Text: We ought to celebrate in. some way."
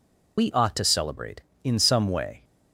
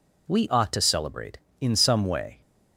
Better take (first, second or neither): second